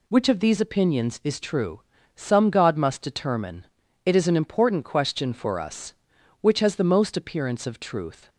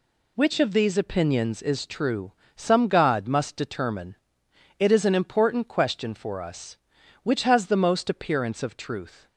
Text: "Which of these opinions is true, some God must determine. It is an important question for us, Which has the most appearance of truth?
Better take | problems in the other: neither | none

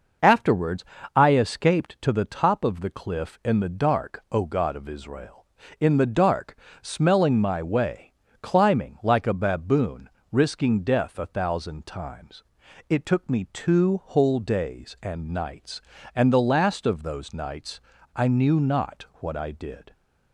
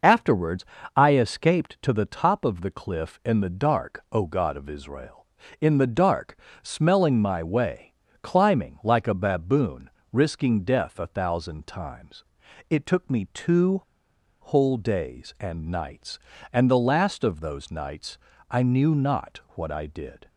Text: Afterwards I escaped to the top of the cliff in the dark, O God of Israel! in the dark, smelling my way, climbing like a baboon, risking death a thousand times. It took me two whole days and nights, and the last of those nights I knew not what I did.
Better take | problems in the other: first | pauses between "Afterwards" and "I"; slight; at 0.6 s; 0.32 s long; slight in the first // pauses between "two" and "whole"; noticeable; at 13.8 s; 0.61 s long // pauses between "nights" and "I"; slight; at 18.1 s; 0.32 s long; slight in the first

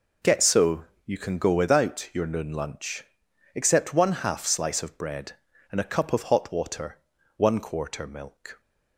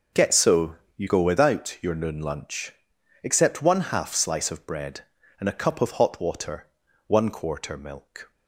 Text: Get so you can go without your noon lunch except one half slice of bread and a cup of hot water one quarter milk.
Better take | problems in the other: first | pauses between "so" and "you"; slight; at 0.7 s; 0.20 s long; slight in the first // skips "can"; at 1.0 s // pauses between "lunch" and "except"; noticeable; at 2.7 s; 0.52 s long; noticeable in the first // pauses between "water" and "one"; at 6.6 s; 0.42 s long; also in the first

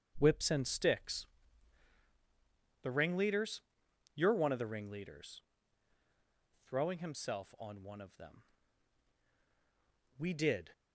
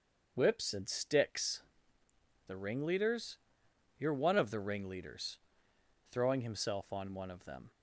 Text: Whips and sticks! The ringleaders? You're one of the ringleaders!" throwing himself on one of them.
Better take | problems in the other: second | starts louder than the rest; until 1.1 s; 7 dB; also in the second // goes on to say "We did"; from 10.1 s on; 0.56 s long

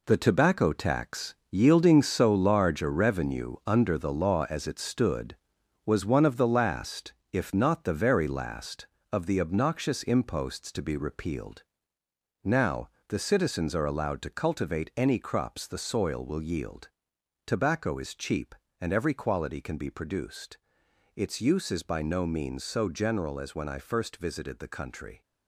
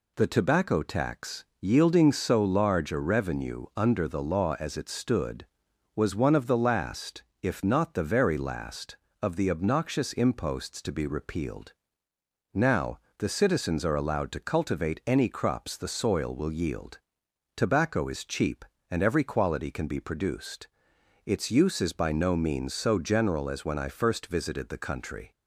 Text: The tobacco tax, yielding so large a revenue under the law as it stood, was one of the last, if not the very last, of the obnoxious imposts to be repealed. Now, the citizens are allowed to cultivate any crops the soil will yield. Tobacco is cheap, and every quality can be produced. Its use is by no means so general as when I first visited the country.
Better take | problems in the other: second | gets quieter; strong; throughout; 9 dB

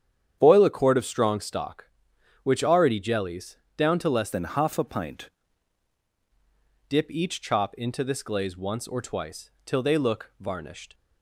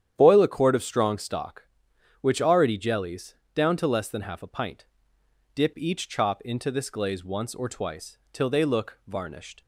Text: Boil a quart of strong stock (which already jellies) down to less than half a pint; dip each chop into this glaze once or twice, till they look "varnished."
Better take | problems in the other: second | starts louder than the rest; strong; until 1.4 s; 9 dB; strong in the second // changes voice from "than" to "pint"; from 4.3 to 5.2 s; 0.9 s long

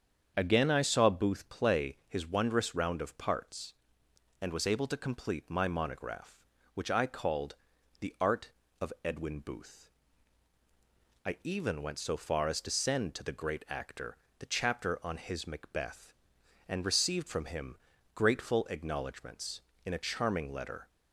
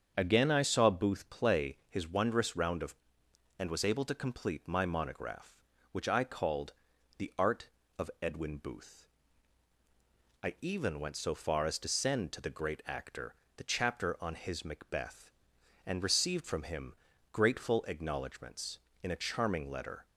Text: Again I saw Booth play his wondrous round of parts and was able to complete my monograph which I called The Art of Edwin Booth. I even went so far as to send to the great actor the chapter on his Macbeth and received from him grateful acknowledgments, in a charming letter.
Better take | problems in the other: first | starts louder than the rest; strong; until 1.1 s; 7.5 dB; strong in the first // skips "parts"; at 3.2 s // pauses between "called" and "The"; at 6.7 s; 0.44 s long; also in the first // pauses between "actor" and "the"; slight; at 13.3 s; 0.22 s long; slight in the first // pauses between "him" and "grateful"; at 16.9 s; 0.38 s long; also in the first

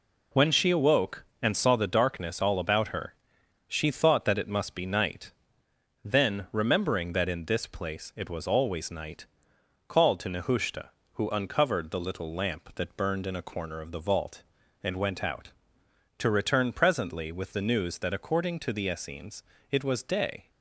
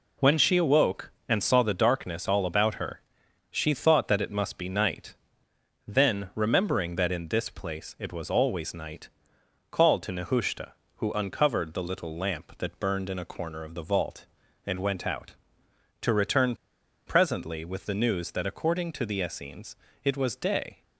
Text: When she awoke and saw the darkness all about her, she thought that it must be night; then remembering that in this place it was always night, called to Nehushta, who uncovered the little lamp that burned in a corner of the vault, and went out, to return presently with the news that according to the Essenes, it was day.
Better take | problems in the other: first | pauses between "return" and "presently"; noticeable; at 16.5 s; 0.50 s long

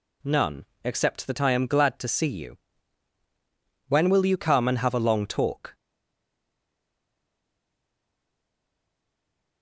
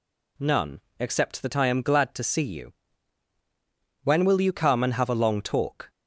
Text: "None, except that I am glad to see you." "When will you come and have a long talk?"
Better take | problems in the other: second | stays silent after the last word; strong; from 5.7 s on; 3.9 s long

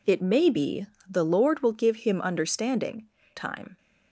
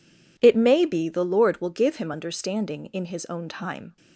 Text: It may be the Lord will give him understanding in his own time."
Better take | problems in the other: second | pauses between "be" and "the"; slight; at 0.8 s; 0.24 s long // skips "in his own"; at 3.2 s

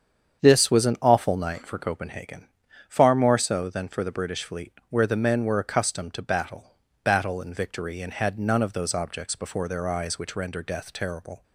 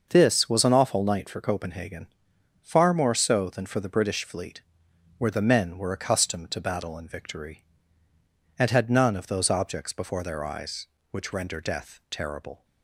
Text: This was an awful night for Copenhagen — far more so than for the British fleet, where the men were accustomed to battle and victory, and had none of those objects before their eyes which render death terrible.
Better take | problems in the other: second | starts louder than the rest; strong; until 1.4 s; 7.5 dB; also in the second // says "battle" twice; at 7.0 s

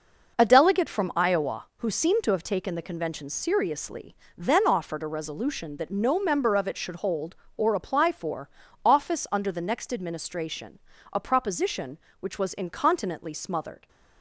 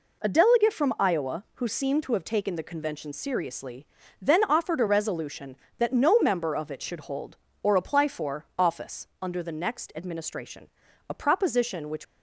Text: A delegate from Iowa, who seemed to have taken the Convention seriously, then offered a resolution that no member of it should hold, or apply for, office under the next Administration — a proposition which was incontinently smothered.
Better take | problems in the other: first | pauses between "office" and "under"; slight; at 9.0 s; 0.16 s long // stops before "was incontinently smothered"; at 12.0 s

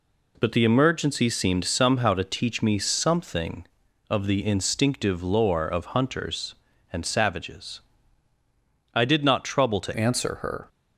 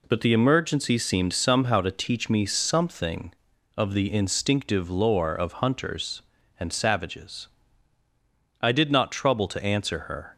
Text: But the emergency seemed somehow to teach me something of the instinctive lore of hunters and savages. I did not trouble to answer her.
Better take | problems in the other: second | changes voice at "answer"; from 9.9 s on; 0.7 s long

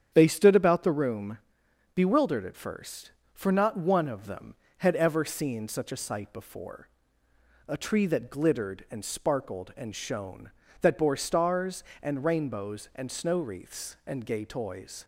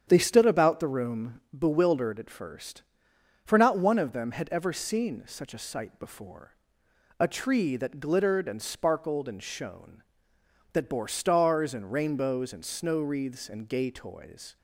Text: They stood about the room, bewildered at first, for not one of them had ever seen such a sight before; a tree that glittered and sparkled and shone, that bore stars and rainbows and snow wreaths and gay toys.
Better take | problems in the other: neither | starts louder than the rest; strong; the same in both

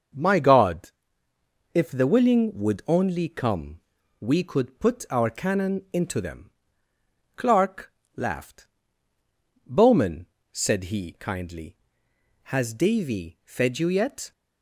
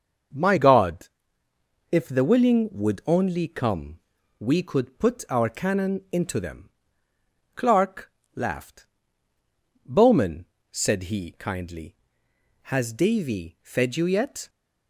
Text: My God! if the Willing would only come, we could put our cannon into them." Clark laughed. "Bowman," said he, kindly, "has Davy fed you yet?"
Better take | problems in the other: neither | starts louder than the rest; noticeable; the same in both // pauses between "Clark" and "laughed"; slight; the same in both

